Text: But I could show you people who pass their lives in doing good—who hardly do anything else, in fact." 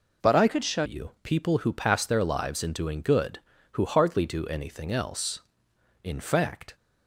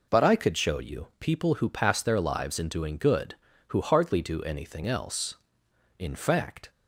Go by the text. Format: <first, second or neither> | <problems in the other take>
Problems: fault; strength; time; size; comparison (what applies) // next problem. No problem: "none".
second | changes voice from "could" to "show"; from 0.4 to 0.8 s; 0.4 s long